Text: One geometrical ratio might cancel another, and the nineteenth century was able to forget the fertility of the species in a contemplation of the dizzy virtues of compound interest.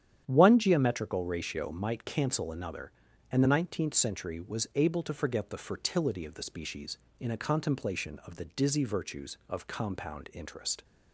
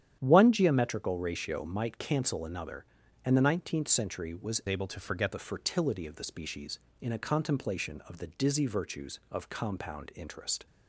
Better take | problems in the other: first | starts louder than the rest; strong; until 1.2 s; 10 dB; strong in the first // changes voice from "able" to "forget"; from 4.6 to 5.3 s; 0.7 s long

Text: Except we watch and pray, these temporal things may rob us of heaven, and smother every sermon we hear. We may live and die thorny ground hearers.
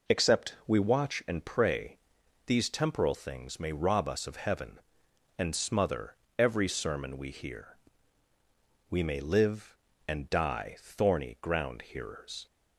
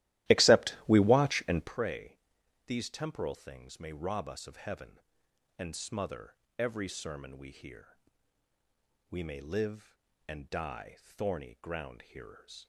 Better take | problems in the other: first | starts louder than the rest; strong; until 1.8 s; 15.5 dB // pauses between "smother" and "every"; slight; at 6.3 s; 0.24 s long; slight in the first

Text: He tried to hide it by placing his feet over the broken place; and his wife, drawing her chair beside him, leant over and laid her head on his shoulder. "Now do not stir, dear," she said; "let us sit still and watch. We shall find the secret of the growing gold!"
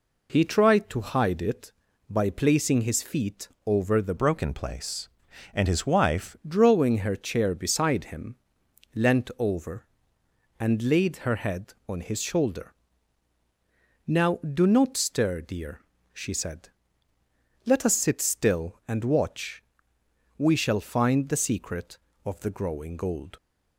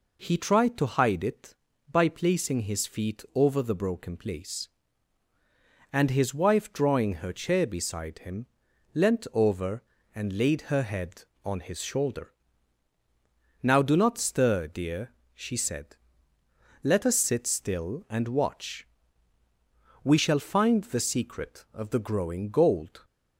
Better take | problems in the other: second | pauses between "feet" and "over"; slight; at 3.4 s; 0.18 s long // changes voice from "broken" to "wife"; from 4.1 to 6.3 s; 2.2 s long

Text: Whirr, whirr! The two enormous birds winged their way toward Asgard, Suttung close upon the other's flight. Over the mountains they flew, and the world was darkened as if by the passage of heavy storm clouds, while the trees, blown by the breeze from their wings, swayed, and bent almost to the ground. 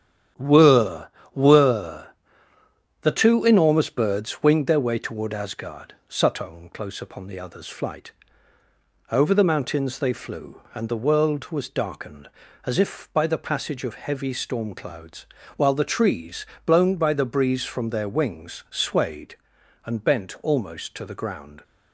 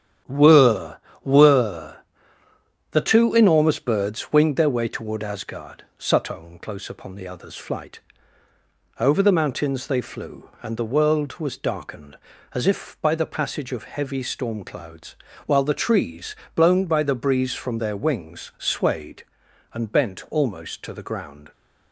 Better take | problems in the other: neither | starts louder than the rest; strong; the same in both

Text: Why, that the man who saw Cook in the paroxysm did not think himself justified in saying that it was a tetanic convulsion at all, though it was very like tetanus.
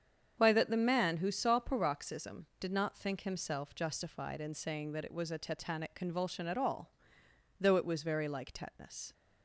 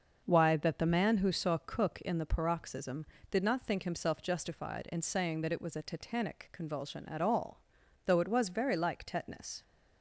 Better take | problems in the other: second | starts louder than the rest; strong; until 1.3 s; 8 dB // skips "Cook in the"; at 1.5 s

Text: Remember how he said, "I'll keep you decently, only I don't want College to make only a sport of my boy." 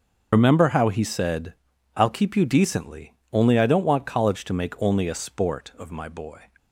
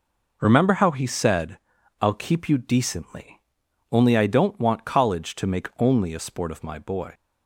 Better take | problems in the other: second | loses the start of "Remember"; at 0.3 s; 90 ms // starts louder than the rest; until 1.3 s; 6.5 dB

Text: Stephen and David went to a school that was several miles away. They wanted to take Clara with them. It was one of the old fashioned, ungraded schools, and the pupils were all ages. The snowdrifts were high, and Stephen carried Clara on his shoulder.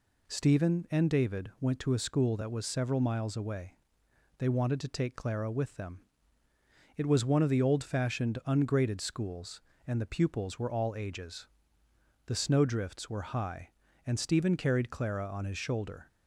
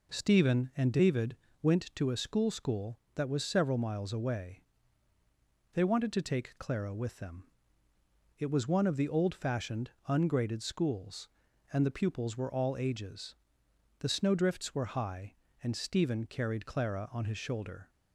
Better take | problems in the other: first | pauses between "David" and "went"; slight; at 1.3 s; 0.26 s long // says "school" twice; at 2.5 s

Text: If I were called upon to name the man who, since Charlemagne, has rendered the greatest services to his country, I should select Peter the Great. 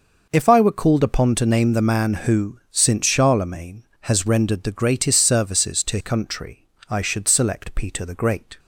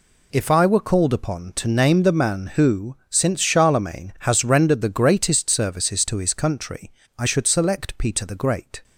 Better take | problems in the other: second | skips "his"; at 5.9 s

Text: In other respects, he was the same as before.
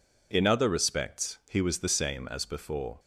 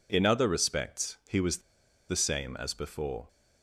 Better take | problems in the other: first | pauses between "was" and "the"; noticeable; at 1.5 s; 0.49 s long

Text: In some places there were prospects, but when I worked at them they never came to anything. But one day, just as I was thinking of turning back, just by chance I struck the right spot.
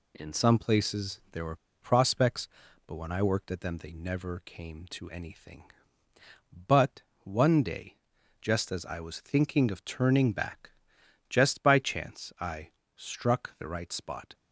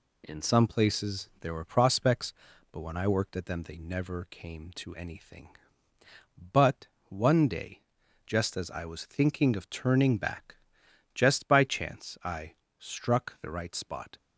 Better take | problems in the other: second | pauses between "were" and "prospects"; slight; at 1.5 s; 0.25 s long // pauses between "But" and "one"; slight; at 7.0 s; 0.18 s long; slight in the second // pauses between "I" and "struck"; slight; at 12.6 s; 0.26 s long; slight in the second

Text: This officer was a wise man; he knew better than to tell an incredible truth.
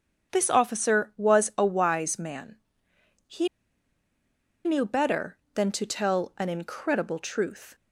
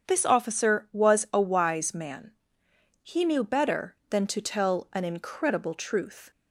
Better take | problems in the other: second | starts louder than the rest; strong; until 1.3 s; 7.5 dB; also in the second // pauses between "he" and "knew"; at 3.4 s; 1.1 s long

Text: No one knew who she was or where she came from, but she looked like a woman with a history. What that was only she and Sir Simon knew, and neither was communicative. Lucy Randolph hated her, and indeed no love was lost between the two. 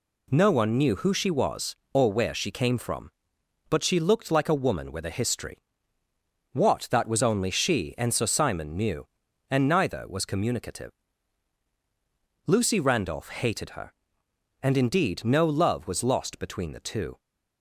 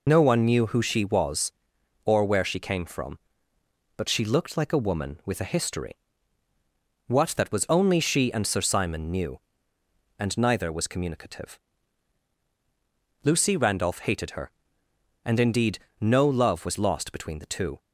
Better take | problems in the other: first | loses the start of "No"; at 0.0 s; 50 ms // pauses between "indeed" and "no"; slight; at 15.7 s; 0.22 s long

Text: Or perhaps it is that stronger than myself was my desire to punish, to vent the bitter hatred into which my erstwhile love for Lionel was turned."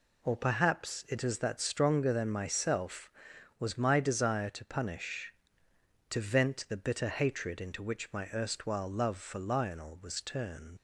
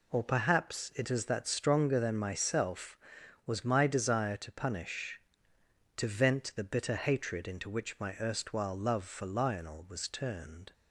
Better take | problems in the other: second | leaves "turned" unfinished; at 10.7 s; 85 ms

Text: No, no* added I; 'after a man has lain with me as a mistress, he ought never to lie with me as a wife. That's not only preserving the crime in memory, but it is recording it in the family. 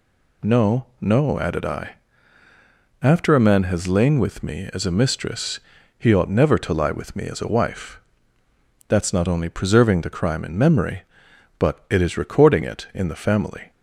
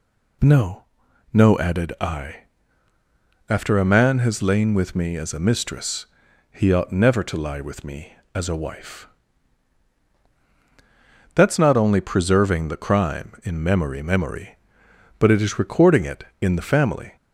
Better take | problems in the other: first | says "memory" twice; at 14.0 s

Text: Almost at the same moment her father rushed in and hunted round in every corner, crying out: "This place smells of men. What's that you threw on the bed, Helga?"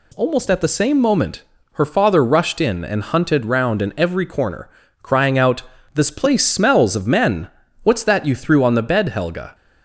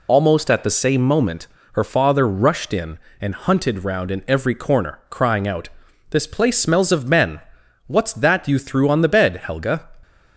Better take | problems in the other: first | loses the start of "Almost"; at 0.0 s; 45 ms // pauses between "moment" and "her"; slight; at 1.4 s; 0.26 s long; slight in the first

